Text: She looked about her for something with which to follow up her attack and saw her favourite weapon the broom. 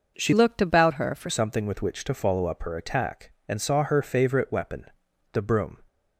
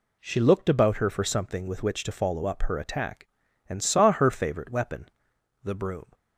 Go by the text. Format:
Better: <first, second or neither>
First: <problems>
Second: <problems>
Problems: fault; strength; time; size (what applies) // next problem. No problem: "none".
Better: second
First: changes voice from "looked" to "for"; from 0.3 to 1.2 s; 0.9 s long // pauses between "weapon" and "the"; noticeable; at 4.8 s; 0.48 s long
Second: pauses between "weapon" and "the"; noticeable; at 5.0 s; 0.52 s long